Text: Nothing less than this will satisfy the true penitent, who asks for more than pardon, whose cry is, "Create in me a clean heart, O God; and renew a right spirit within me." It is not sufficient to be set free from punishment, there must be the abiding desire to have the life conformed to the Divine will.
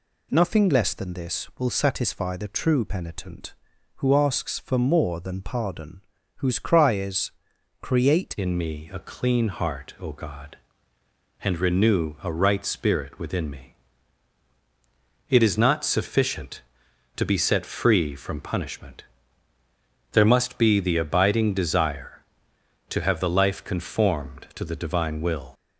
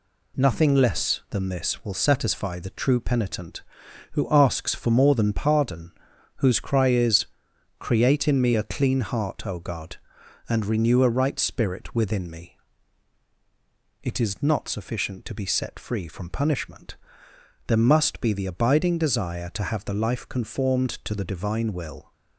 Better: second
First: changes voice at "in"; from 8.3 s on; 17.2 s long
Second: none

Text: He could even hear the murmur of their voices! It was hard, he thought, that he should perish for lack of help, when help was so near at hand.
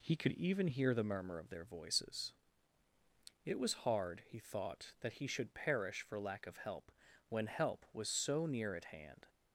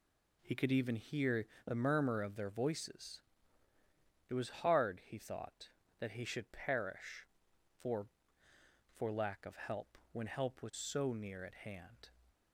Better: first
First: none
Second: pauses between "hear" and "the"; slight; at 1.4 s; 0.18 s long // says "for" twice; at 8.9 s

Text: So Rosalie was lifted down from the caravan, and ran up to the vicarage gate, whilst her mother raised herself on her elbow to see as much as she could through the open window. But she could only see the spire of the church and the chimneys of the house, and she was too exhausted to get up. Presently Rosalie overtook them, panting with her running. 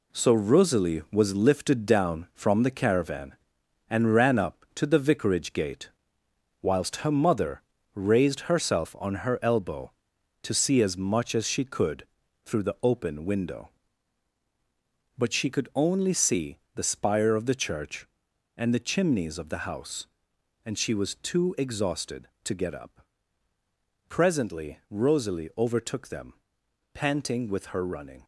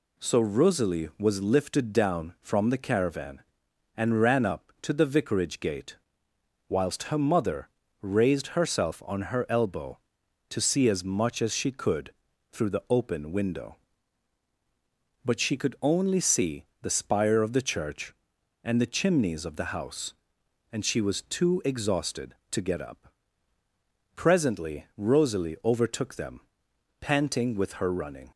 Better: second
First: gets quieter; throughout; 6.5 dB // pauses between "mother" and "raised"; slight; at 7.6 s; 0.32 s long // pauses between "could" and "through"; at 12.0 s; 0.38 s long // pauses between "see" and "the"; slight; at 16.5 s; 0.16 s long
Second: pauses between "mother" and "raised"; slight; at 7.6 s; 0.32 s long // pauses between "could" and "through"; at 12.1 s; 0.38 s long // pauses between "see" and "the"; slight; at 16.6 s; 0.16 s long

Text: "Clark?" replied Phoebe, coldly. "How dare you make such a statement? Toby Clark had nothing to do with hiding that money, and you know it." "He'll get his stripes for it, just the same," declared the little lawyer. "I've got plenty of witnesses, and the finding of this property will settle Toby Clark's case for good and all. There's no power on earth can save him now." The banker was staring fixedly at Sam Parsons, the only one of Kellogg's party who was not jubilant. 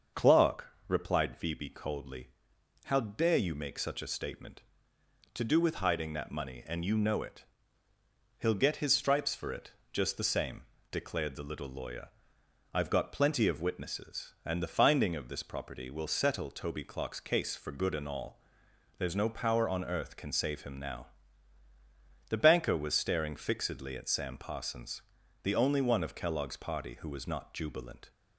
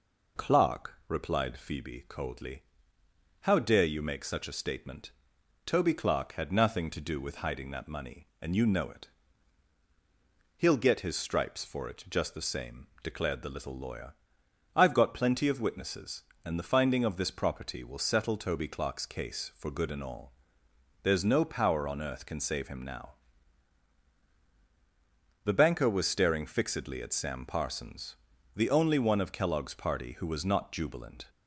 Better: second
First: starts louder than the rest; until 1.3 s; 6.5 dB // skips "Toby Clark had nothing"; at 4.9 s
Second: none

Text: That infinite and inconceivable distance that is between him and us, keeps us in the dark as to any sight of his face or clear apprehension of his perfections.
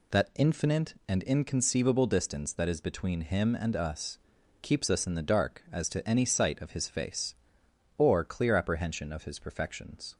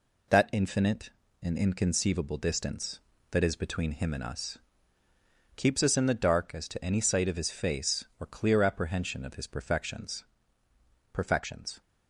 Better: first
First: none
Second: says "perfections" twice; at 11.1 s

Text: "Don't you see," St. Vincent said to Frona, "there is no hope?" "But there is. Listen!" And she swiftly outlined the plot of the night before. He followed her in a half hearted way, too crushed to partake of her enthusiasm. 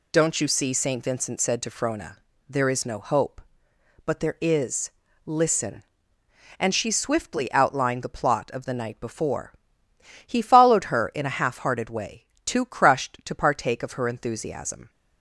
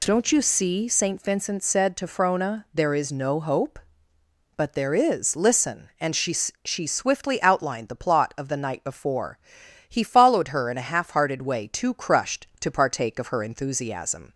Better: first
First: none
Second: says "she" twice; at 6.6 s

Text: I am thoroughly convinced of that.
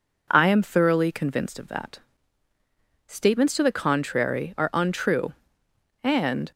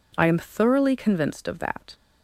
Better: second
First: goes on to say "Statements to the contrary are untrue and"; strong; from 3.0 s on; 3.4 s long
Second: none

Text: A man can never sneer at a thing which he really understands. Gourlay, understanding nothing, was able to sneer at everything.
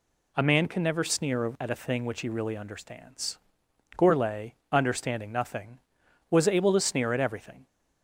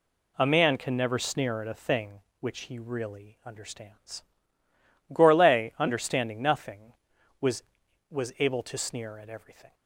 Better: first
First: none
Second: says "was" twice; at 8.0 s

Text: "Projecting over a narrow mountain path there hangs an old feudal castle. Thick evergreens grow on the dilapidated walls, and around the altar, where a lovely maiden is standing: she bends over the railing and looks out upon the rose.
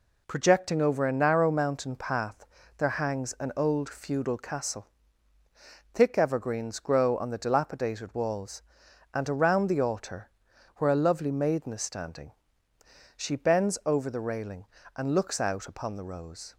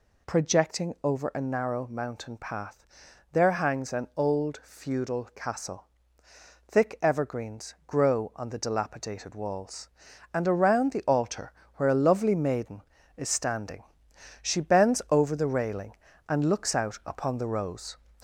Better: first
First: pauses between "path" and "there"; slight; at 2.4 s; 0.32 s long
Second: gets louder; slight; throughout; 2.5 dB // pauses between "path" and "there"; noticeable; at 2.8 s; 0.46 s long

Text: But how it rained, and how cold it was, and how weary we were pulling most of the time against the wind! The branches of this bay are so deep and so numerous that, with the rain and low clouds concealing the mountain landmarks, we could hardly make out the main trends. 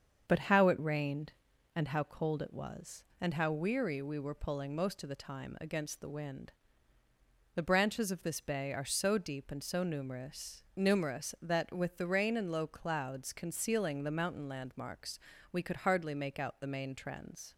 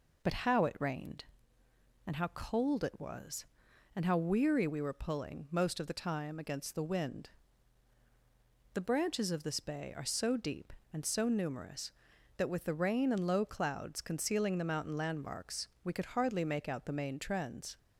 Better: second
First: starts louder than the rest; until 1.2 s; 7 dB // says "numerous" twice; at 10.7 s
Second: none

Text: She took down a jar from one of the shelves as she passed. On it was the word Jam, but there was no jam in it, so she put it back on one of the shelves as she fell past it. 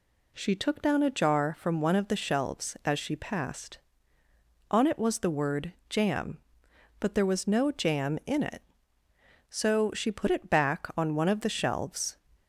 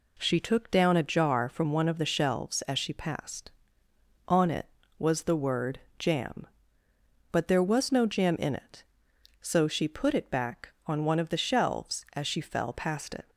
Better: second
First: pauses between "word" and "Jam"; slight; at 5.7 s; 0.16 s long // stops before "as she fell past it"; at 12.3 s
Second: pauses between "word" and "Jam"; slight; at 5.7 s; 0.20 s long

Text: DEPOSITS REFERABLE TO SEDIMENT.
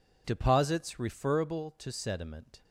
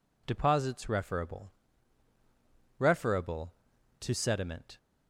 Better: first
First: none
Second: says "REFERABLE" twice; at 2.7 s

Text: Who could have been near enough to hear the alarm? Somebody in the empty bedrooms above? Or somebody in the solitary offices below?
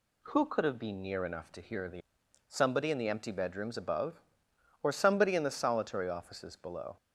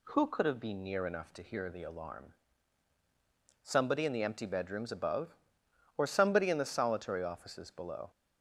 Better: second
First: skips "alarm"; at 2.2 s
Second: none

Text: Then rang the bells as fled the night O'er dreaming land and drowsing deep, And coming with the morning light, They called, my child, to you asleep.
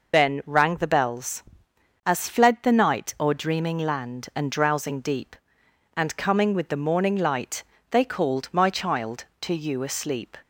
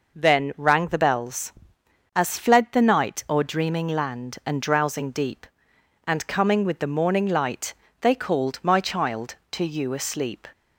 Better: second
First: loses the start of "Then"; at 0.1 s; 105 ms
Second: none

